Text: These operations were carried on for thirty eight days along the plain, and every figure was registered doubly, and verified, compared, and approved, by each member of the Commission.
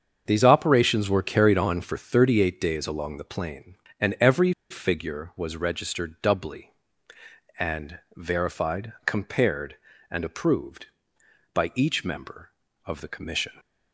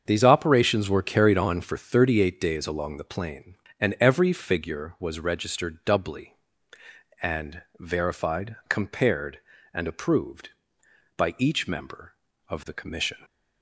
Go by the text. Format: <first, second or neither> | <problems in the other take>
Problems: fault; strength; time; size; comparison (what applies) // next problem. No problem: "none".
second | starts louder than the rest; until 1.2 s; 7 dB; also in the second // pauses between "every" and "figure"; slight; at 4.5 s; 0.19 s long // pauses between "and" and "verified"; slight; at 7.9 s; 0.18 s long; slight in the second